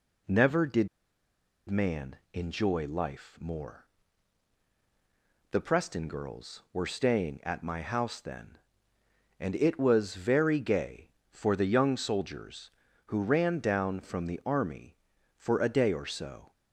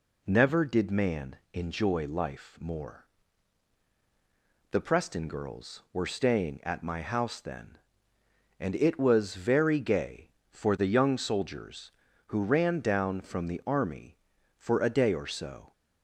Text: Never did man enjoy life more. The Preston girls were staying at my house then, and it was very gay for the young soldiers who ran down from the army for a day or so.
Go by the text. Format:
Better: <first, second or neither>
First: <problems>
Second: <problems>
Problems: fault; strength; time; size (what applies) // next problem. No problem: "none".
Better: second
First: pauses between "did" and "man"; noticeable; at 0.8 s; 0.80 s long // pauses between "man" and "enjoy"; slight; at 2.1 s; 0.18 s long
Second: pauses between "man" and "enjoy"; slight; at 1.3 s; 0.18 s long